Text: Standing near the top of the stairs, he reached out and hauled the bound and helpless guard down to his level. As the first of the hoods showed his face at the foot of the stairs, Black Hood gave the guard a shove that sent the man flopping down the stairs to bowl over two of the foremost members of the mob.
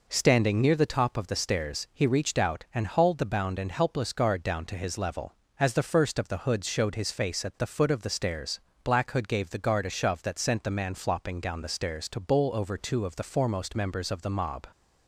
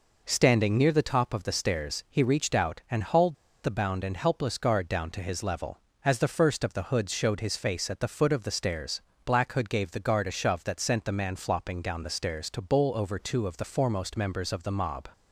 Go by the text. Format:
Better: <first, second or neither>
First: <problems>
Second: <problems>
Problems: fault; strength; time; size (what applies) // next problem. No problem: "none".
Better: first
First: none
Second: pauses between "hauled" and "the"; slight; at 3.3 s; 0.30 s long